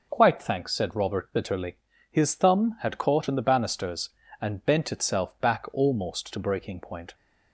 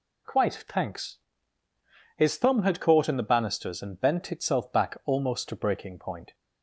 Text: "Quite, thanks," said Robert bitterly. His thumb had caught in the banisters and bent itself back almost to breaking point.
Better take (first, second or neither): first